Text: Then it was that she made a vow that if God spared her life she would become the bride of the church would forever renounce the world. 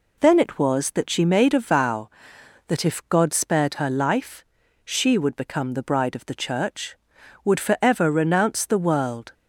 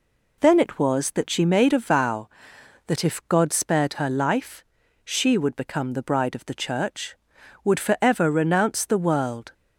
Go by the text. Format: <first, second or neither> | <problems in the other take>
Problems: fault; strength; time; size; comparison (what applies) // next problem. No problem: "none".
neither | pauses between "life" and "she"; the same in both